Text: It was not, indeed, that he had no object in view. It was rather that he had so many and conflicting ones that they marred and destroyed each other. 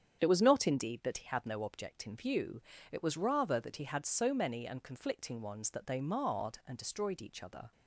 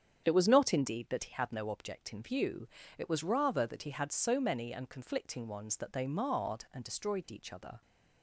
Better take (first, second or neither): neither